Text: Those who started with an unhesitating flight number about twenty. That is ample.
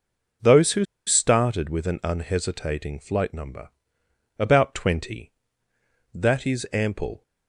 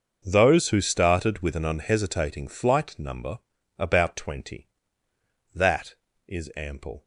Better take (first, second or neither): second